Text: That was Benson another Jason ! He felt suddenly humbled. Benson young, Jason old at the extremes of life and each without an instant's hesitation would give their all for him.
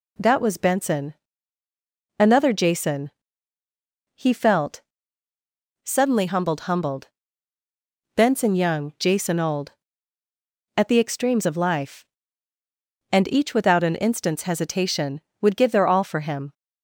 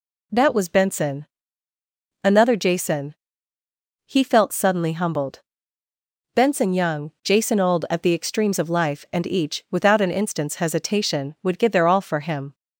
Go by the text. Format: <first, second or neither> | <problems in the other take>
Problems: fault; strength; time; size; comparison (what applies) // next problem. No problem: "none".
second | pauses between "Benson" and "another"; at 1.1 s; 1.0 s long; noticeable in the second // pauses between "felt" and "suddenly"; at 4.7 s; 1.0 s long // says "humbled" twice; at 6.6 s